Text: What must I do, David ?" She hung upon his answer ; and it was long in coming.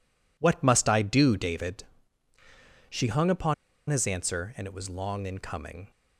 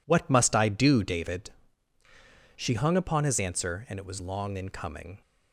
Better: second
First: pauses between "upon" and "his"; slight; at 3.5 s; 0.35 s long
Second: none

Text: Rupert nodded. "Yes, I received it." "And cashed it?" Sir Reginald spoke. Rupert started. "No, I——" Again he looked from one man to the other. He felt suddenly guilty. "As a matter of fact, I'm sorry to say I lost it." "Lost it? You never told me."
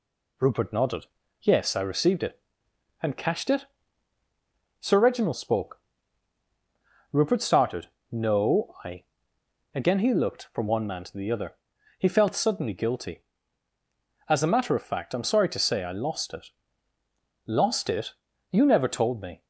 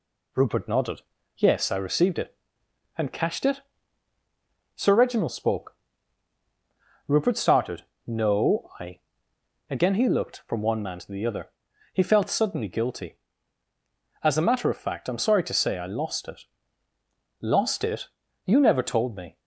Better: neither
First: none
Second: none

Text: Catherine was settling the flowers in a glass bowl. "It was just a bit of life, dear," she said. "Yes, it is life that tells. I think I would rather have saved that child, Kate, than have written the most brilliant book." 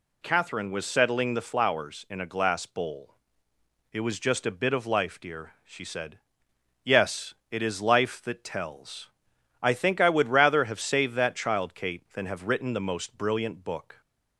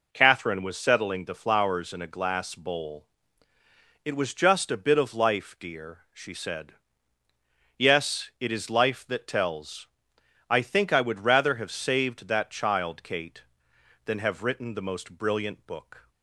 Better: neither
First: none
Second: none

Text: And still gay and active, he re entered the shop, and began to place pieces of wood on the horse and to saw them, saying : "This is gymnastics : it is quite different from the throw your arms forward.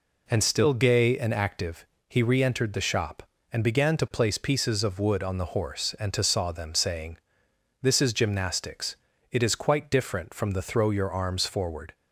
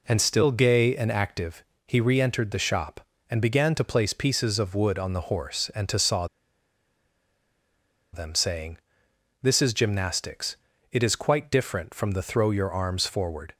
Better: first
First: none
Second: pauses between "saw" and "them"; strong; at 6.2 s; 1.8 s long

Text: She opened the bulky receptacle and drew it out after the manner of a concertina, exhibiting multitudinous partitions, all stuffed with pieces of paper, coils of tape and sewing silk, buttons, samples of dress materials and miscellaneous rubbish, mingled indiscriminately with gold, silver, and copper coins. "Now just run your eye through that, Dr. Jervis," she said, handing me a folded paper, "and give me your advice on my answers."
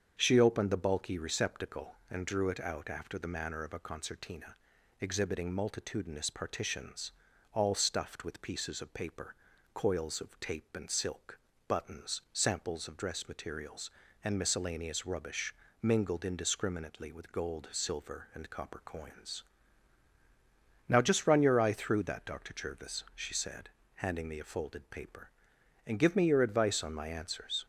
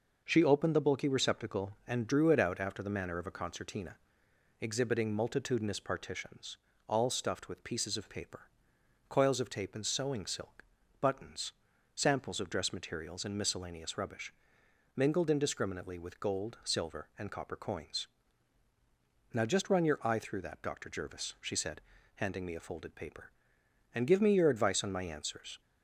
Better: second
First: starts louder than the rest; strong; until 1.1 s; 7.5 dB // skips "sewing"; at 10.8 s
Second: none

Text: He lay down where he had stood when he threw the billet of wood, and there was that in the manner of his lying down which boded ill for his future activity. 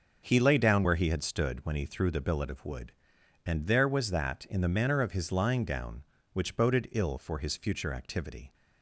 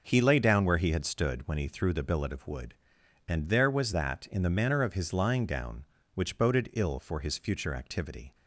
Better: neither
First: starts louder than the rest; until 1.2 s; 6 dB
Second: starts louder than the rest; noticeable; until 1.0 s; 6 dB

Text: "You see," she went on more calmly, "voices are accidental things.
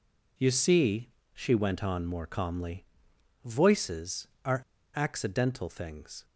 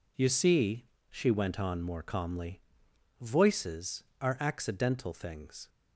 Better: second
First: pauses between "are" and "accidental"; slight; at 4.6 s; 0.34 s long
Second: none

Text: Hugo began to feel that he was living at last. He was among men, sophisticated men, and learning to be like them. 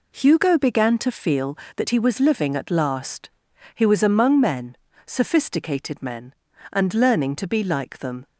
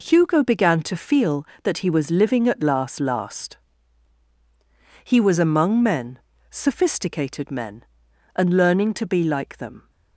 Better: first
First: none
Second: says "last" twice; at 2.9 s

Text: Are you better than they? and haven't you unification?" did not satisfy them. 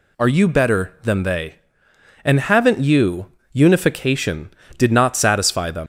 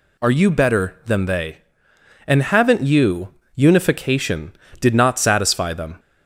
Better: second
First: pauses between "you" and "unification"; slight; at 3.3 s; 0.18 s long // leaves "them" unfinished; at 5.8 s; 105 ms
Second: pauses between "you" and "unification"; slight; at 3.3 s; 0.18 s long

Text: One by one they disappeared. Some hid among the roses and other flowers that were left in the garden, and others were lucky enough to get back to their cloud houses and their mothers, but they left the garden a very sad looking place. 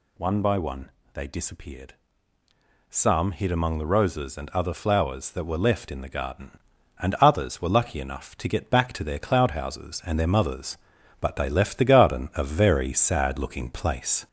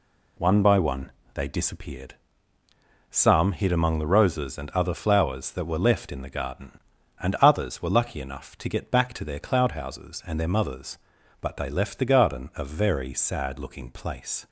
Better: second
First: gets louder; throughout; 3.5 dB // pauses between "one" and "they"; slight; at 0.8 s; 0.24 s long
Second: pauses between "one" and "they"; slight; at 1.0 s; 0.24 s long

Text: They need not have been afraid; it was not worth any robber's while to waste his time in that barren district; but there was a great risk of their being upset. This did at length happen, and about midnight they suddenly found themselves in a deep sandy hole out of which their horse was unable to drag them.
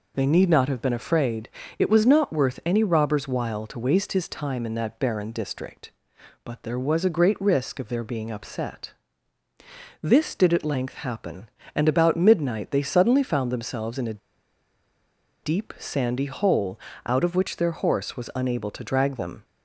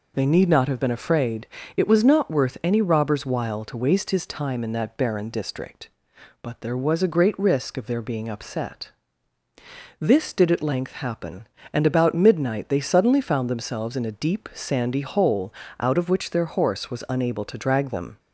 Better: second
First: pauses between "a" and "deep"; at 14.2 s; 1.2 s long // pauses between "hole" and "out"; slight; at 16.7 s; 0.30 s long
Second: pauses between "hole" and "out"; slight; at 15.4 s; 0.30 s long

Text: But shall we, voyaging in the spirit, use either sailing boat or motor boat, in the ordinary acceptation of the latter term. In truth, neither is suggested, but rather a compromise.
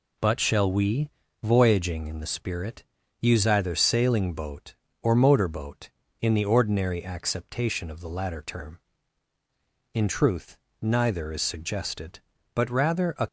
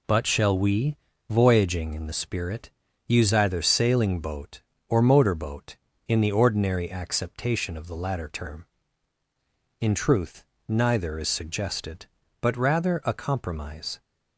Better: second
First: stops before "compromise"; at 13.2 s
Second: none

